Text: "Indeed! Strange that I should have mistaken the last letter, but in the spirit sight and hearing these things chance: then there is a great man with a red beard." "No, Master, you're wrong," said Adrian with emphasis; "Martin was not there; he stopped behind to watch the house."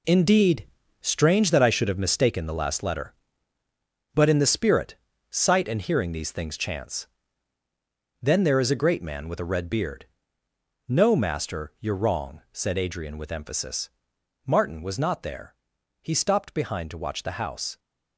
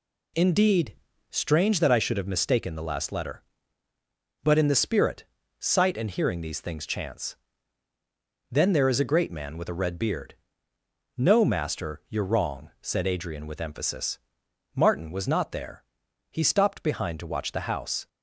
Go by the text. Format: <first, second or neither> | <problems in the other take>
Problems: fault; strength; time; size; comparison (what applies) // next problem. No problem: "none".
second | gets quieter; strong; throughout; 8.5 dB // pauses between "spirit" and "sight"; slight; at 4.9 s; 0.34 s long; slight in the second